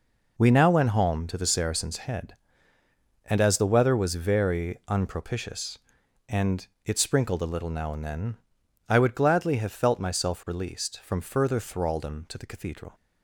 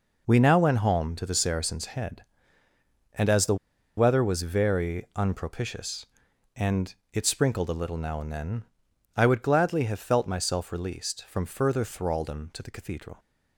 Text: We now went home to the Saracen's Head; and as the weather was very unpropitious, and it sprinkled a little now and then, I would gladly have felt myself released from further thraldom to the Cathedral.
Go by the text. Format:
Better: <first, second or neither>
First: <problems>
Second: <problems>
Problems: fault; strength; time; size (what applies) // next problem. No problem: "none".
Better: first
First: pauses between "and" and "it"; slight; at 6.6 s; 0.18 s long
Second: pauses between "the" and "weather"; at 3.5 s; 0.42 s long // pauses between "and" and "it"; slight; at 6.9 s; 0.18 s long